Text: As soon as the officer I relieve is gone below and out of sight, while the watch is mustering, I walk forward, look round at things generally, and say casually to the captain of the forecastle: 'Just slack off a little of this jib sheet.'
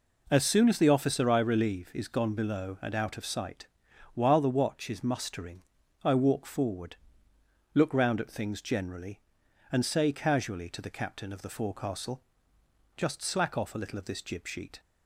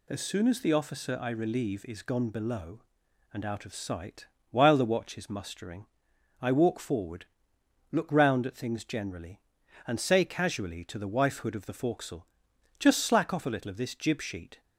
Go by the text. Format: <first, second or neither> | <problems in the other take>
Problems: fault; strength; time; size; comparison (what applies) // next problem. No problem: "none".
first | says "wifehood" for "captain"; at 11.0 s